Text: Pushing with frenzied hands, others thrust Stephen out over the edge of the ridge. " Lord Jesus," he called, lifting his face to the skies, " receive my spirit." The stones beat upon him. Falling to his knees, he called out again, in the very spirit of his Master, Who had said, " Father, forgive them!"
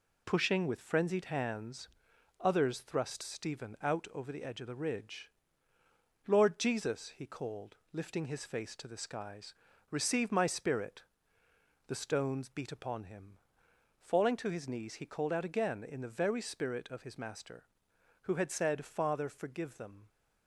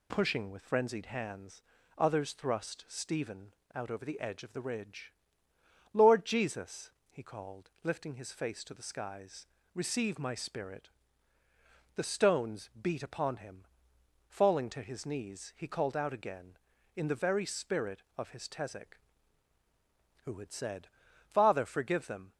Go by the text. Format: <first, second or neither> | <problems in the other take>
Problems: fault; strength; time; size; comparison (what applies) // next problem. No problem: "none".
first | pauses between "Stephen" and "out"; slight; at 3.5 s; 0.20 s long // says "Tezek" for "Master"; at 18.4 s